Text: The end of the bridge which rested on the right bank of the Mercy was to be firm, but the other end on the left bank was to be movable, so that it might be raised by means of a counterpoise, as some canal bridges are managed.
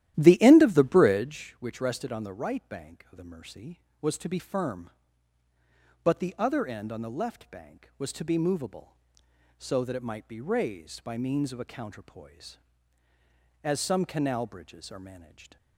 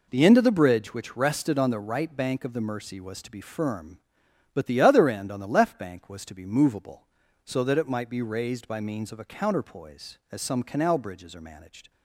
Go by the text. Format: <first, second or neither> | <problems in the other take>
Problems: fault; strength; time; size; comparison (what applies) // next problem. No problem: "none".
second | starts louder than the rest; strong; until 1.4 s; 13 dB